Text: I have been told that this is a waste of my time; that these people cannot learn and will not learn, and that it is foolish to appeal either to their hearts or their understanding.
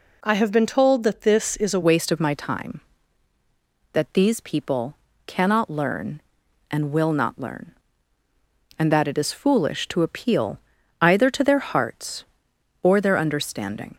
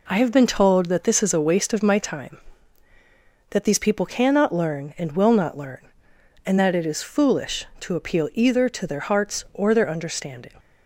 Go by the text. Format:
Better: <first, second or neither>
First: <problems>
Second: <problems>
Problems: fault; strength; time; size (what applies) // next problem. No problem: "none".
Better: second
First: changes voice at "waste"; from 1.8 s on; 12.1 s long // pauses between "people" and "cannot"; slight; at 4.9 s; 0.30 s long // pauses between "appeal" and "either"; at 10.5 s; 0.42 s long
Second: none